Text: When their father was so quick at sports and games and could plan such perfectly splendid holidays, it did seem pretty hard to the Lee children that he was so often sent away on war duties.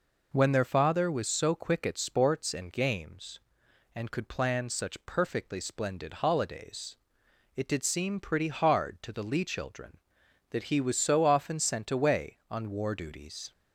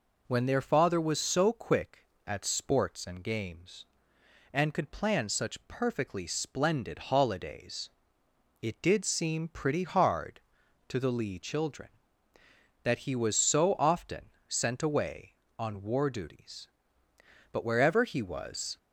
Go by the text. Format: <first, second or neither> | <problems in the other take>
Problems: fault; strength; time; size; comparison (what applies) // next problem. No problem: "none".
first | pauses between "often" and "sent"; slight; at 14.2 s; 0.18 s long // goes on to say "But wherever he was"; noticeable; from 17.5 s on; 1.2 s long